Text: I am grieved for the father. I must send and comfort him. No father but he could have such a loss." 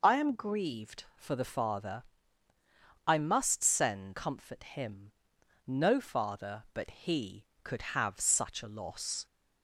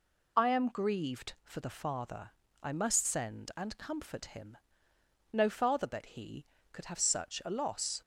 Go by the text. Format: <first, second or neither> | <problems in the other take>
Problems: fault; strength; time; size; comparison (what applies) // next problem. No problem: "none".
second | skips "and"; at 4.1 s